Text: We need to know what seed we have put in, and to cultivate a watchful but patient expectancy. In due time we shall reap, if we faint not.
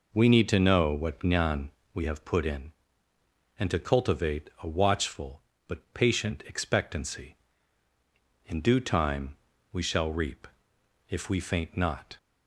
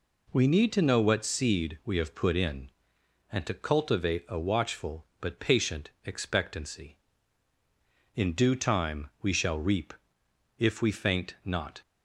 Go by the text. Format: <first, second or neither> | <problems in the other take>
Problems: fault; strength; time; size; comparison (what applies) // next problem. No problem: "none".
second | says "jnan" for "seed"; at 1.1 s // pauses between "time" and "we"; slight; at 9.3 s; 0.36 s long